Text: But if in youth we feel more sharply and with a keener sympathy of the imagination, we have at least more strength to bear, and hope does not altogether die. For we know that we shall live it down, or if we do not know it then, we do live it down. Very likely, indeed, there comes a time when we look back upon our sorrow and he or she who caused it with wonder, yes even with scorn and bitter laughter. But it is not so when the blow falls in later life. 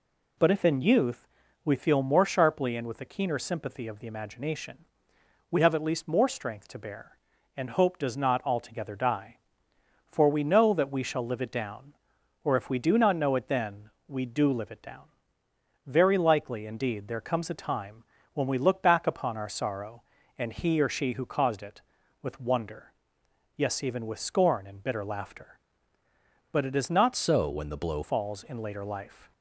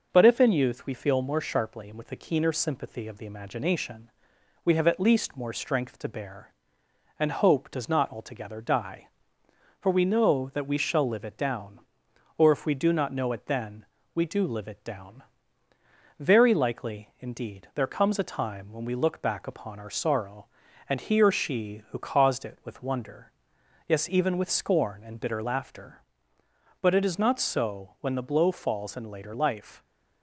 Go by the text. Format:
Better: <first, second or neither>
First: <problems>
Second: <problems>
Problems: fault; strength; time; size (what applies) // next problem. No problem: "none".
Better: second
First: pauses between "youth" and "we"; at 1.2 s; 0.38 s long // pauses between "time" and "when"; slight; at 18.0 s; 0.28 s long // changes voice from "so" to "blow"; from 27.1 to 28.0 s; 0.9 s long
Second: none